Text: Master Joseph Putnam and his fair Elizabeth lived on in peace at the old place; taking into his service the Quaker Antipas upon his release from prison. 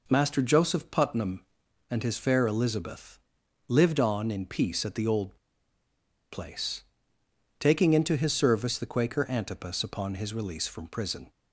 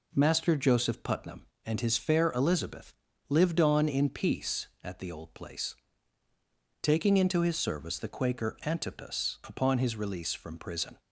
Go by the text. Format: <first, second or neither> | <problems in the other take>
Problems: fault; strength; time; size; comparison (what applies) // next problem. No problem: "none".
second | pauses between "Elizabeth" and "lived"; noticeable; at 3.1 s; 0.48 s long; slight in the second // pauses between "old" and "place"; noticeable; at 5.3 s; 0.94 s long